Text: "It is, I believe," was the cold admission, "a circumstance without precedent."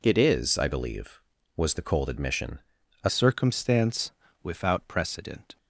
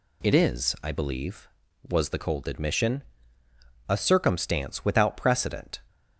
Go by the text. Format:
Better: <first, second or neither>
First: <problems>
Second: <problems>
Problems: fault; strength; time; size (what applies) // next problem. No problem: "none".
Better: second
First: changes voice at "circumstance"; from 3.0 s on; 2.5 s long // pauses between "circumstance" and "without"; slight; at 4.1 s; 0.28 s long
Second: none